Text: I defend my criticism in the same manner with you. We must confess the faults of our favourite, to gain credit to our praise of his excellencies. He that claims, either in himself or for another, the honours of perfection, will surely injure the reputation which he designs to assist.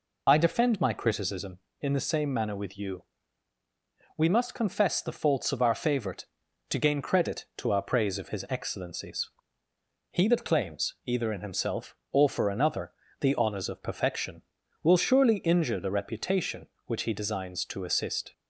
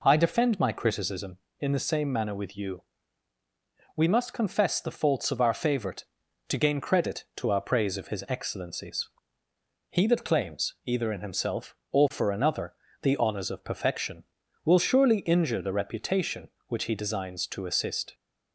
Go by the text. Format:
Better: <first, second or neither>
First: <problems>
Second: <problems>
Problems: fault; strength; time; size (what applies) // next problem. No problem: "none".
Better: second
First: loses the start of "I"; at 0.2 s; 50 ms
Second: none